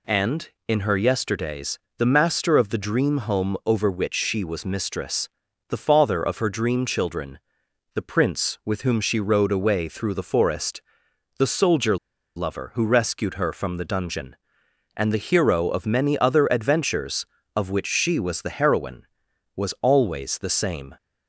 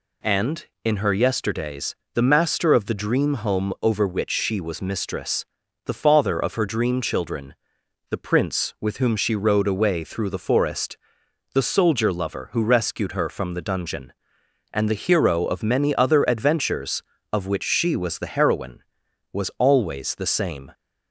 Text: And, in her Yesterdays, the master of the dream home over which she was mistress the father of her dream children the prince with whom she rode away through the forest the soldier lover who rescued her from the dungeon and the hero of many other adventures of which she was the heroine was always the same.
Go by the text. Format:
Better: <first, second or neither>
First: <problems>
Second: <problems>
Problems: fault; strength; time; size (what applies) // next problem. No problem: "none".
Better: second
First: pauses between "mistress" and "the"; at 5.2 s; 0.42 s long // pauses between "children" and "the"; noticeable; at 7.3 s; 0.54 s long // pauses between "forest" and "the"; noticeable; at 10.8 s; 0.56 s long // pauses between "soldier" and "lover"; at 11.9 s; 0.40 s long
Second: pauses between "mistress" and "the"; at 5.4 s; 0.42 s long // pauses between "children" and "the"; noticeable; at 7.5 s; 0.54 s long // pauses between "forest" and "the"; noticeable; at 10.9 s; 0.56 s long